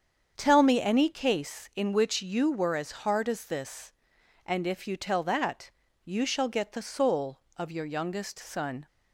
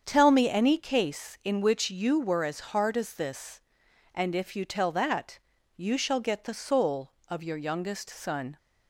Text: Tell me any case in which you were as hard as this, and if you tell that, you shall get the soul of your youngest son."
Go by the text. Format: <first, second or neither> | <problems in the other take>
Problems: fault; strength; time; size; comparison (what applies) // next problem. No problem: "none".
neither | starts louder than the rest; strong; the same in both